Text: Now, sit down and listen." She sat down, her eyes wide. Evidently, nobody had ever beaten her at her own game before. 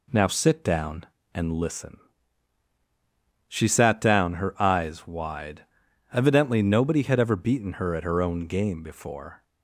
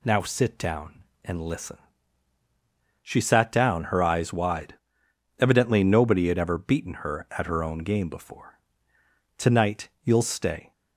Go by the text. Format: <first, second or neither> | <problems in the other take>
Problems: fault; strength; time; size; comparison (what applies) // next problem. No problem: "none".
first | goes on to say "Tonight you'll stay"; from 9.3 s on; 1.3 s long